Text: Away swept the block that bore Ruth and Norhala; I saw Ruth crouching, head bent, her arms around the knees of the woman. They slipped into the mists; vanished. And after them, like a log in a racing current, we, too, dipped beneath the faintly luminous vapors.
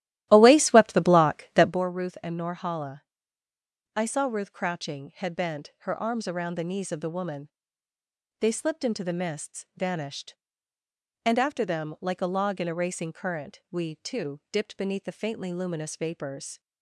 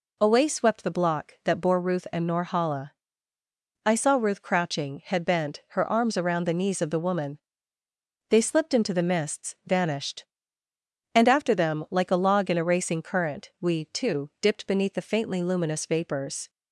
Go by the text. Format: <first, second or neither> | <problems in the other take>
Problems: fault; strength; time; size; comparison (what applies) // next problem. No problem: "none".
second | starts louder than the rest; strong; until 1.8 s; 14 dB